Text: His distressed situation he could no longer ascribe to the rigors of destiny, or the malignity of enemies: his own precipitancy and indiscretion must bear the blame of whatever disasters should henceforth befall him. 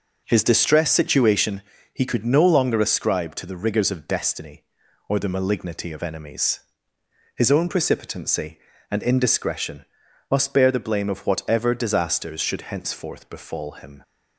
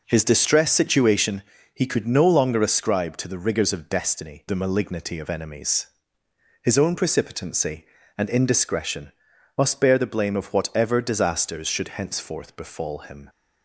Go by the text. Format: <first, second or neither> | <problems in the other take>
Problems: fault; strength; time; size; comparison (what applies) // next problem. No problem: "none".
first | pauses between "situation" and "he"; slight; at 1.4 s; 0.32 s long; slight in the first // skips "or"; at 4.4 s // pauses between "indiscretion" and "must"; noticeable; at 9.1 s; 0.48 s long; noticeable in the first